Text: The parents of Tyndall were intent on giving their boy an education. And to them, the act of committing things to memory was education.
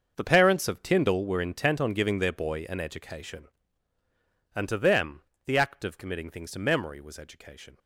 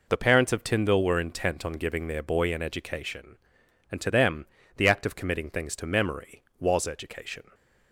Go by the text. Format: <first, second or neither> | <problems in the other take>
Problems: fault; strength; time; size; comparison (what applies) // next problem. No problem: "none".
second | gets quieter; strong; throughout; 14.5 dB